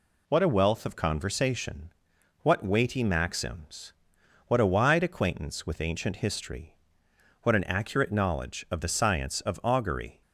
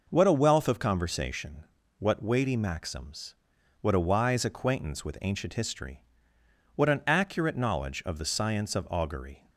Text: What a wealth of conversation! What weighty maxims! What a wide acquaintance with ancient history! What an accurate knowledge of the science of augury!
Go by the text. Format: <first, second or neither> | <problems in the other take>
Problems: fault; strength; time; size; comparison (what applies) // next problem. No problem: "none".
first | says "wise" for "wide"; at 3.9 s